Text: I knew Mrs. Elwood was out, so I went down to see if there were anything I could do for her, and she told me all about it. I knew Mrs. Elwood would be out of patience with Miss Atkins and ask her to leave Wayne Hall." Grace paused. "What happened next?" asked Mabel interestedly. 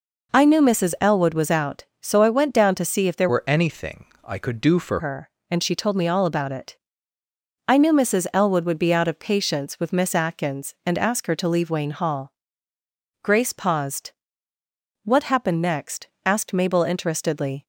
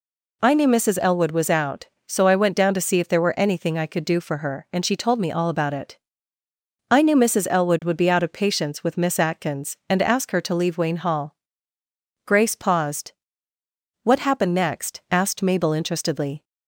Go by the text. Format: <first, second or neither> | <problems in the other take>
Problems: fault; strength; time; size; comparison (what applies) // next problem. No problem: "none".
second | changes voice from "were" to "for"; from 3.2 to 5.0 s; 1.8 s long // pauses between "anything" and "I"; slight; at 4.0 s; 0.22 s long